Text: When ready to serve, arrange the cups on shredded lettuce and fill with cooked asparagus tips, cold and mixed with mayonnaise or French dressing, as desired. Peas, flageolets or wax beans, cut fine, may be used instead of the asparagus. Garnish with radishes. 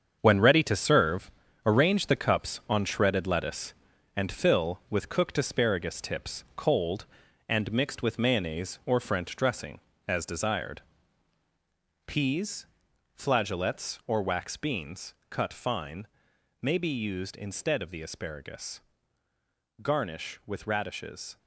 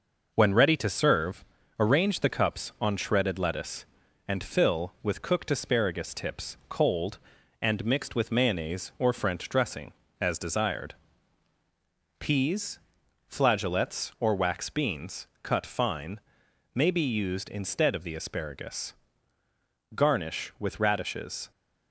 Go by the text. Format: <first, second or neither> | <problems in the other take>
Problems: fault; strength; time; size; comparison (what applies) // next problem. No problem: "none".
second | gets quieter; strong; throughout; 8.5 dB